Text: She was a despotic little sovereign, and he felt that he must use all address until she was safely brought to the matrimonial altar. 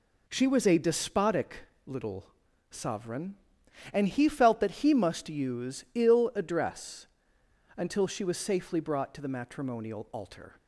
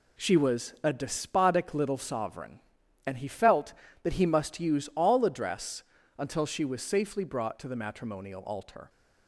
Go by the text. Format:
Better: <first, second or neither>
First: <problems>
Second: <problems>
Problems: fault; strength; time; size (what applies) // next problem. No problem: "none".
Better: second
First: pauses between "despotic" and "little"; slight; at 1.5 s; 0.26 s long // pauses between "little" and "sovereign"; at 2.2 s; 0.42 s long // says "ill" for "all"; at 5.9 s // pauses between "address" and "until"; noticeable; at 7.0 s; 0.70 s long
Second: pauses between "address" and "until"; slight; at 5.8 s; 0.34 s long